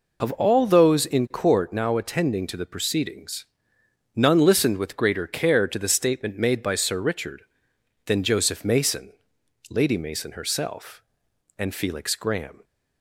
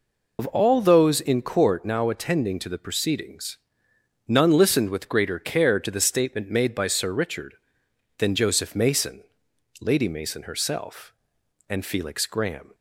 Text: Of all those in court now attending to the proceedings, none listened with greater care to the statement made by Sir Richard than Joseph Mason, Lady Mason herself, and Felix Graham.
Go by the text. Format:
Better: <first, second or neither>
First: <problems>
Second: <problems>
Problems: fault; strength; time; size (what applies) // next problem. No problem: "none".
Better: first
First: none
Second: loses the start of "Of"; at 0.3 s; 45 ms